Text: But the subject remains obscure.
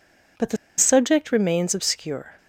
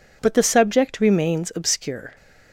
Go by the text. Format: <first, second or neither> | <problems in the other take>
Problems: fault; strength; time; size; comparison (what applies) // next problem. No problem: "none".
second | pauses between "the" and "subject"; slight; at 0.5 s; 0.22 s long